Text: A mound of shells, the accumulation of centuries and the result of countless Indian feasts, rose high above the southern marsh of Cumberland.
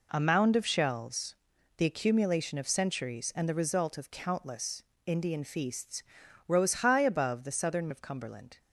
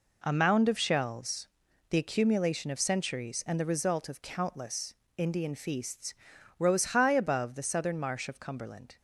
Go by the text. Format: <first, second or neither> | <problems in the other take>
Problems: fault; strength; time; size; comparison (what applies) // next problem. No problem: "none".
second | pauses between "countless" and "Indian"; slight; at 4.8 s; 0.24 s long; slight in the second // skips "marsh"; at 7.8 s